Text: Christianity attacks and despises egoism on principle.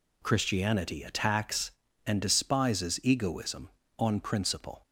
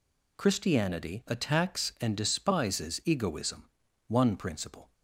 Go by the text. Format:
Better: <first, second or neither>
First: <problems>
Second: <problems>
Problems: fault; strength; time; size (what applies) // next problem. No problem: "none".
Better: first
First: none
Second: says "one" for "on"; at 4.0 s